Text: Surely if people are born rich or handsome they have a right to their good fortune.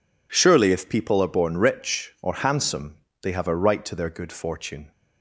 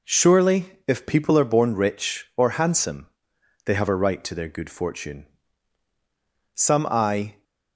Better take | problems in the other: first | pauses between "handsome" and "they"; noticeable; at 3.0 s; 0.58 s long; slight in the first // goes on to say "Some I"; noticeable; from 6.5 s on; 0.88 s long

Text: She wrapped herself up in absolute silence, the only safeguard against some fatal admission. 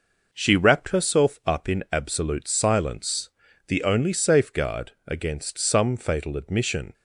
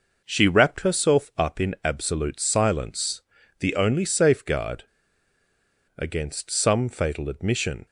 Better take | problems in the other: first | pauses between "safeguard" and "against"; at 4.8 s; 1.1 s long

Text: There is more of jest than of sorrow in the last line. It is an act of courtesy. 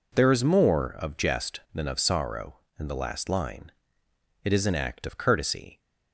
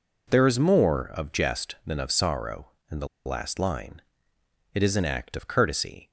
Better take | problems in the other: first | pauses between "the" and "last"; slight; at 3.0 s; 0.19 s long

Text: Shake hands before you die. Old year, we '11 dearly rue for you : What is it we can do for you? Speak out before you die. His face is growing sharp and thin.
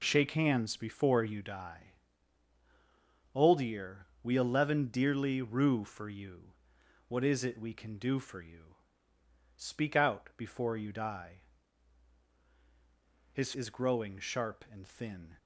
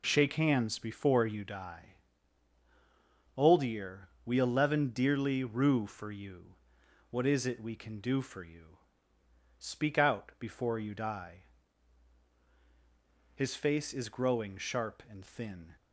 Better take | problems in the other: second | skips "face"; at 13.5 s

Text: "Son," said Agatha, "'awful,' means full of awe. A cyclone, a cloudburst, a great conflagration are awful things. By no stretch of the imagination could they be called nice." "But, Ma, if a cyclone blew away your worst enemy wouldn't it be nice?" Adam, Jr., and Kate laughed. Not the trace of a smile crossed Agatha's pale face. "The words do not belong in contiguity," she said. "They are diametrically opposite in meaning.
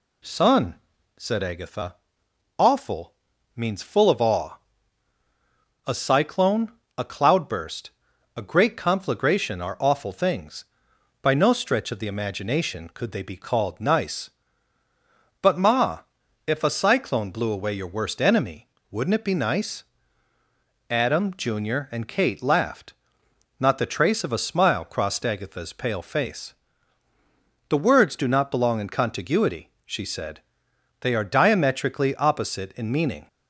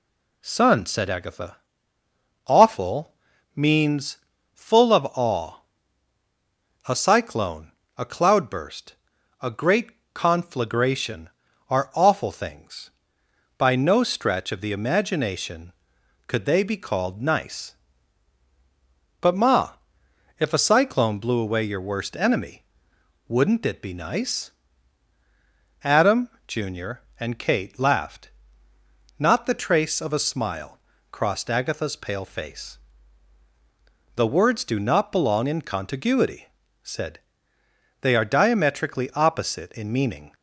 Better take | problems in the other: first | pauses between "means" and "full"; slight; at 4.1 s; 0.36 s long // pauses between "great" and "conflagration"; slight; at 9.9 s; 0.22 s long // pauses between "enemy" and "wouldn't"; noticeable; at 22.6 s; 0.62 s long; slight in the first // pauses between "smile" and "crossed"; slight; at 30.7 s; 0.32 s long // skips "she"; at 36.6 s

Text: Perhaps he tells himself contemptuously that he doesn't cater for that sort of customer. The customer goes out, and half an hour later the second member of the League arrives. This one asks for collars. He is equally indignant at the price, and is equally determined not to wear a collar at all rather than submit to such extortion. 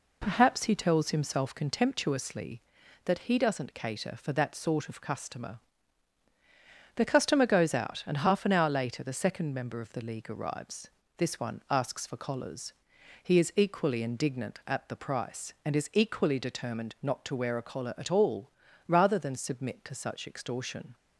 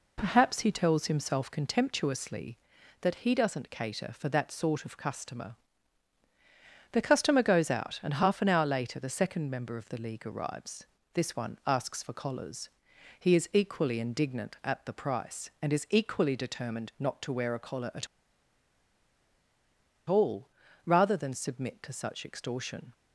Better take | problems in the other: first | pauses between "at" and "all"; strong; at 18.0 s; 2.0 s long // pauses between "all" and "rather"; slight; at 20.4 s; 0.36 s long; slight in the first

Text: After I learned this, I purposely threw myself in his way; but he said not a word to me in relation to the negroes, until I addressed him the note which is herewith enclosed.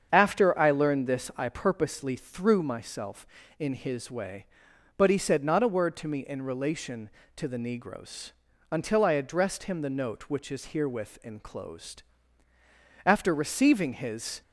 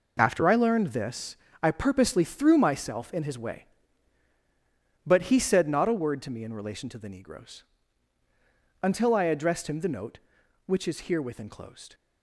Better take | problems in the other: second | starts louder than the rest; strong; until 1.1 s; 7.5 dB // goes on to say "After receiving his"; from 13.0 s on; 1.3 s long

